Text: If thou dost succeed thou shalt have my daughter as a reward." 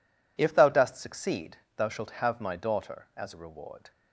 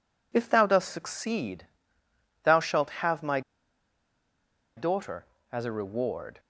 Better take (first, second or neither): first